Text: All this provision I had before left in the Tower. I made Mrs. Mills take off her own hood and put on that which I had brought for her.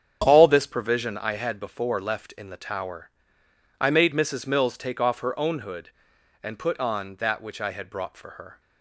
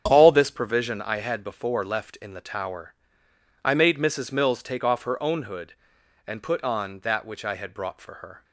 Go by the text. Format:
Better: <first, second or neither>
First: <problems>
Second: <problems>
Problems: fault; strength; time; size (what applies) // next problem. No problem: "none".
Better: neither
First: starts louder than the rest; strong; until 1.2 s; 8 dB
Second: starts louder than the rest; strong; until 1.0 s; 8 dB